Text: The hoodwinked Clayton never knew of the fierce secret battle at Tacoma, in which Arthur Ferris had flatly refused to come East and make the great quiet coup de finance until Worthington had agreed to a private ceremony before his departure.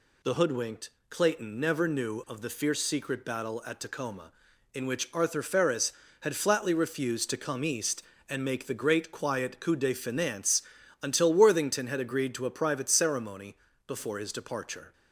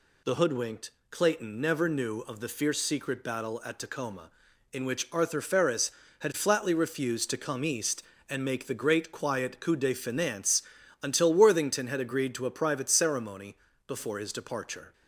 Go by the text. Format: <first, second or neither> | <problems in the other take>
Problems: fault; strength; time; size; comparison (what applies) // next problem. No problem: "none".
neither | pauses between "hoodwinked" and "Clayton"; slight; the same in both // pauses between "finance" and "until"; the same in both // pauses between "ceremony" and "before"; slight; the same in both